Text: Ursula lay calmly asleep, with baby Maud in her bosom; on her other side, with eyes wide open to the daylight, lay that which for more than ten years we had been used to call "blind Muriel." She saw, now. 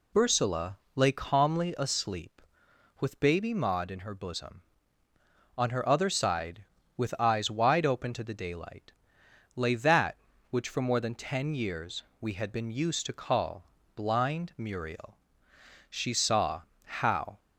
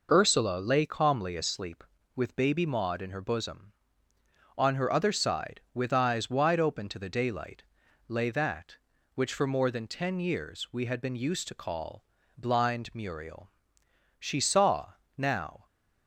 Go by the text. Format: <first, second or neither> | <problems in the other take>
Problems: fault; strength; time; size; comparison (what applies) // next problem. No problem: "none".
second | pauses between "Ursula" and "lay"; slight; at 0.7 s; 0.20 s long // pauses between "years" and "we"; slight; at 12.0 s; 0.16 s long // pauses between "call" and "blind"; slight; at 13.6 s; 0.32 s long; slight in the second // says "how" for "now"; at 16.8 s